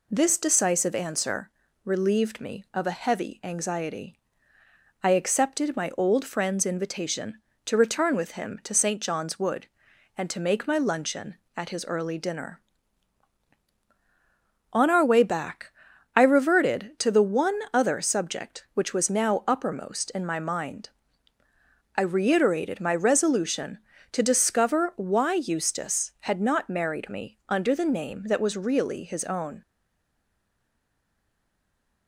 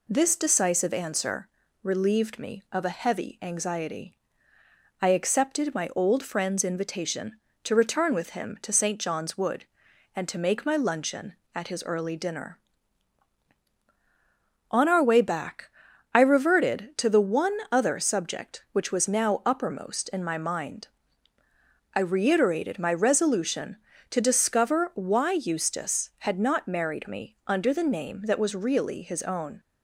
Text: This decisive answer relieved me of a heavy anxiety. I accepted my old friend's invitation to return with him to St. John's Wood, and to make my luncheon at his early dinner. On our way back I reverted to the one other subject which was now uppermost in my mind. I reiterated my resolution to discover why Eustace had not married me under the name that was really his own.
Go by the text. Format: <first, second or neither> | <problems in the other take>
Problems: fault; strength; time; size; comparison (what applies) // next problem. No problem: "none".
second | pauses between "answer" and "relieved"; slight; at 1.5 s; 0.32 s long; slight in the second // pauses between "back" and "I"; noticeable; at 15.6 s; 0.48 s long; noticeable in the second // stays silent after the last word; from 29.6 s on; 2.4 s long